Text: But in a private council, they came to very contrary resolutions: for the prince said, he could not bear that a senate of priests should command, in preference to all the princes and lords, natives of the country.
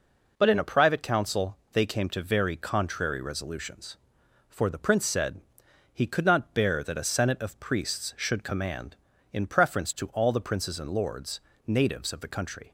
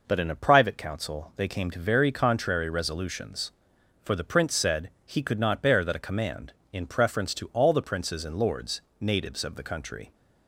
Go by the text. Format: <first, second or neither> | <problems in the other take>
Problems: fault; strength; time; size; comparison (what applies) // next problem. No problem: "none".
first | skips "senate of priests should"; at 6.0 s